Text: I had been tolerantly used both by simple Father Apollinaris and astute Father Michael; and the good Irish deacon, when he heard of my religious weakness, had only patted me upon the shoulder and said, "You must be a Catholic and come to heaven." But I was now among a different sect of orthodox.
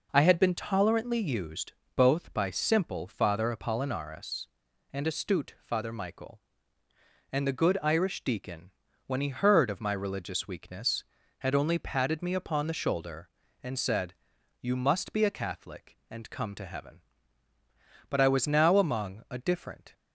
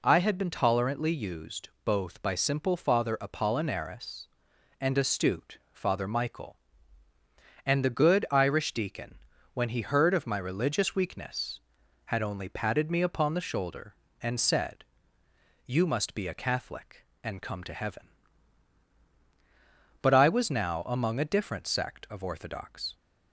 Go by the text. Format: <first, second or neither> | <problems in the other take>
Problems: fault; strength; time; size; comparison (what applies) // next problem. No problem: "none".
second | pauses between "used" and "both"; slight; at 1.7 s; 0.22 s long // stops before "sect of orthodox"; at 19.9 s